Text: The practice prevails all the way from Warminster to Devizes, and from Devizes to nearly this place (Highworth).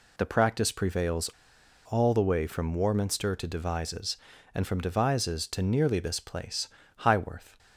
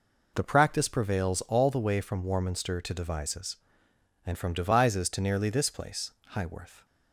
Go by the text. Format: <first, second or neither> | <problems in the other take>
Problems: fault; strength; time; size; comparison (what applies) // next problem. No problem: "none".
second | pauses between "prevails" and "all"; noticeable; at 1.2 s; 0.61 s long